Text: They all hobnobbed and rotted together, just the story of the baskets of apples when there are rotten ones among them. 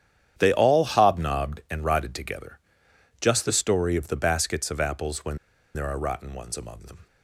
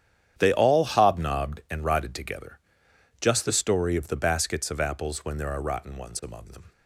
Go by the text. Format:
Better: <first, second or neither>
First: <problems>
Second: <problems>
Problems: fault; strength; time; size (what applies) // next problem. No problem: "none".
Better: second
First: starts louder than the rest; strong; until 1.3 s; 9.5 dB // pauses between "when" and "there"; at 5.3 s; 0.37 s long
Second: starts louder than the rest; strong; until 1.3 s; 9.5 dB